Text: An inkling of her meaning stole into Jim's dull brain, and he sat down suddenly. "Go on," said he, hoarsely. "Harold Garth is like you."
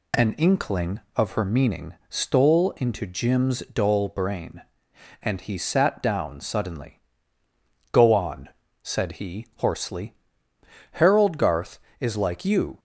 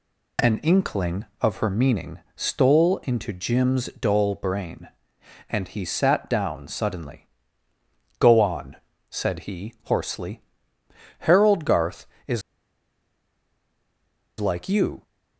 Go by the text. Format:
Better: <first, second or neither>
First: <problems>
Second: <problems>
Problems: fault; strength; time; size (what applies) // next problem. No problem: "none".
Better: first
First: none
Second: pauses between "is" and "like"; strong; at 12.4 s; 1.9 s long